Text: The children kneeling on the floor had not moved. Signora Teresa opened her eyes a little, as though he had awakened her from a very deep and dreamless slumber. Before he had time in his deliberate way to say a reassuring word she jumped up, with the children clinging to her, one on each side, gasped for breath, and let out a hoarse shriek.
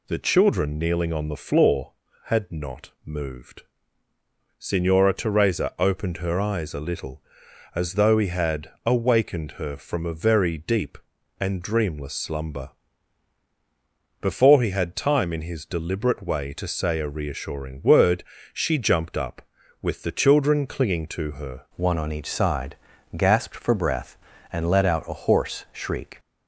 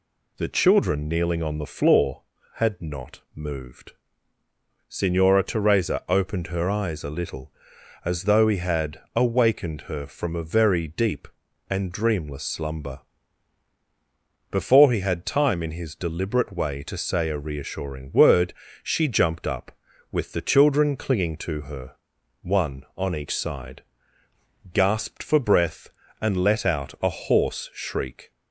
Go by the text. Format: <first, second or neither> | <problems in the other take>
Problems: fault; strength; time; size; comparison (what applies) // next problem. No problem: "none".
second | pauses between "word" and "she"; slight; at 18.2 s; 0.30 s long; slight in the second // changes voice at "one"; from 21.7 s on; 4.4 s long